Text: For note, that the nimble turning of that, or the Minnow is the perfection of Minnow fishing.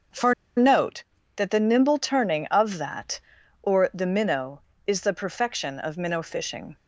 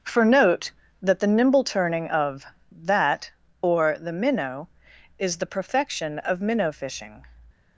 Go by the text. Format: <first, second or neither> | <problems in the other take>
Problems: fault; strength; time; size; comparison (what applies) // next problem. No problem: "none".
second | starts louder than the rest; until 1.7 s; 6.5 dB; also in the second // pauses between "For" and "note"; slight; at 0.3 s; 0.23 s long